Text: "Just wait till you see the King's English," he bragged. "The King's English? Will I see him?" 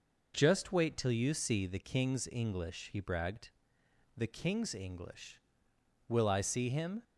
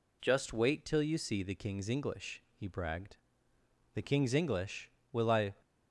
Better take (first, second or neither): first